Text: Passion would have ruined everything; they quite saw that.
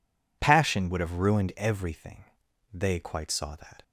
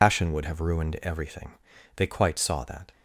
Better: first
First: none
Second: loses the start of "Passion"; at 0.0 s; 105 ms

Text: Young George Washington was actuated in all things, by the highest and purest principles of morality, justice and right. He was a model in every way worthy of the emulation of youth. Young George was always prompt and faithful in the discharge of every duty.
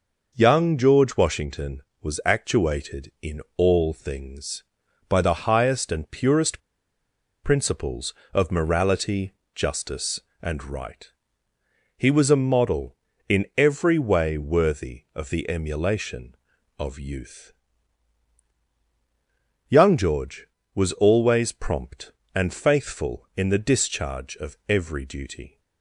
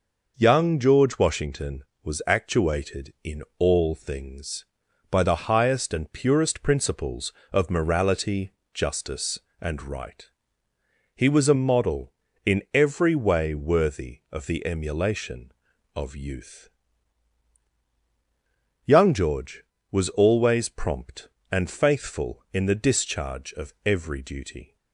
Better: second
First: pauses between "in" and "all"; slight; at 3.4 s; 0.16 s long // pauses between "purest" and "principles"; noticeable; at 6.5 s; 0.85 s long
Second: pauses between "in" and "all"; slight; at 3.4 s; 0.16 s long

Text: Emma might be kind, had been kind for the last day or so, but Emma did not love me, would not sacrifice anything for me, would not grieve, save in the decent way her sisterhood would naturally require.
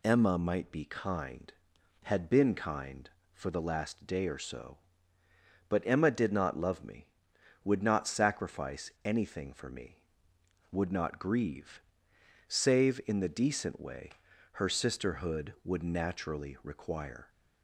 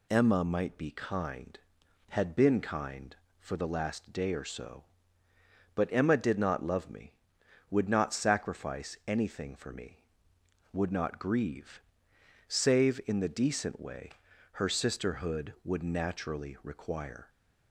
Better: neither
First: pauses between "way" and "her"; at 14.0 s; 0.44 s long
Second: pauses between "way" and "her"; at 14.0 s; 0.44 s long

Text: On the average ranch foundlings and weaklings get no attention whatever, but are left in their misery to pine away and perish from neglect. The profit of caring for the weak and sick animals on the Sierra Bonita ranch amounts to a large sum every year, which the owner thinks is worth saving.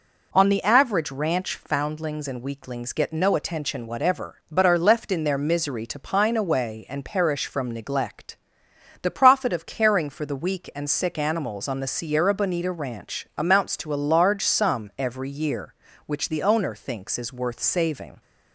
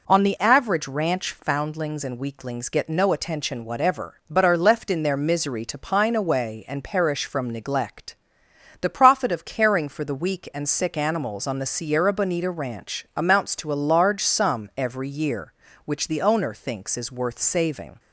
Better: neither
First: none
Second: none

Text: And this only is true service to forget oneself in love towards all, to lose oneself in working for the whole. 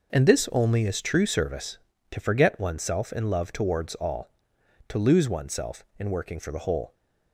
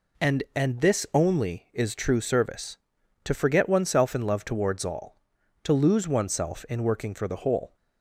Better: first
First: none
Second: says "And" twice; at 0.5 s

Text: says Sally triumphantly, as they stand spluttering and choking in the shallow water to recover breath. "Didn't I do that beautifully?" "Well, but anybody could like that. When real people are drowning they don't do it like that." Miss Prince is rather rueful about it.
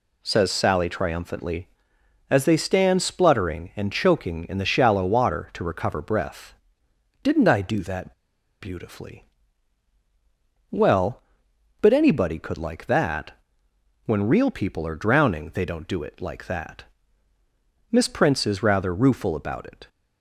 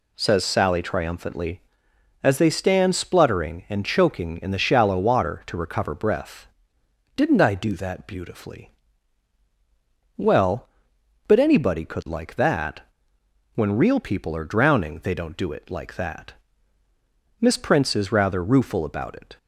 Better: second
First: pauses between "that" and "beautifully"; noticeable; at 8.1 s; 0.47 s long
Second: none

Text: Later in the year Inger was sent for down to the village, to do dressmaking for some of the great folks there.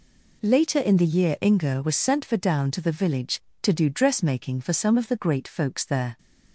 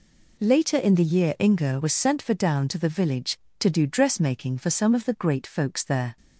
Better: neither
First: none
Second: none

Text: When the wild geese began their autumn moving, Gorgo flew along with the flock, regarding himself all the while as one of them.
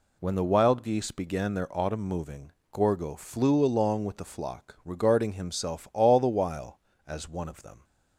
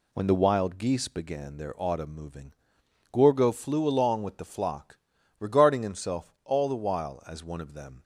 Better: neither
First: none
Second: none

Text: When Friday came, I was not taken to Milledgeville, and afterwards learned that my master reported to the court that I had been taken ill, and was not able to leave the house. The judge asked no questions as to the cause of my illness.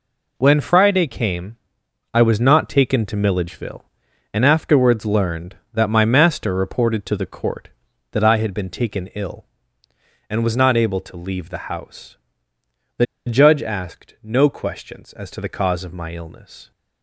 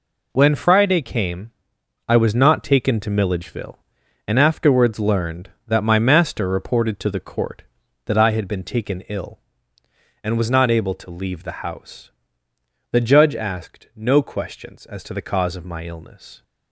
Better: second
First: pauses between "The" and "judge"; slight; at 13.0 s; 0.21 s long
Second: none

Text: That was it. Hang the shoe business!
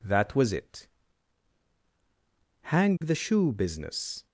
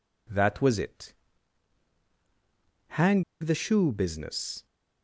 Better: first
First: none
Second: pauses between "Hang" and "the"; slight; at 3.2 s; 0.18 s long

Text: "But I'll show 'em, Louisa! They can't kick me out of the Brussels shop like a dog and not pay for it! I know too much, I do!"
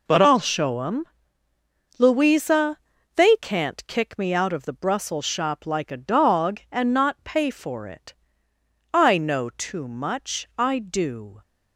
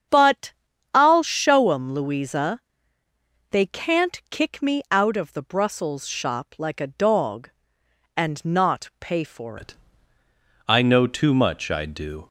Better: first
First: none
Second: starts louder than the rest; strong; until 1.5 s; 8 dB // pauses between "But" and "I'll"; at 0.5 s; 0.42 s long // changes voice at "it"; from 9.5 s on; 2.7 s long

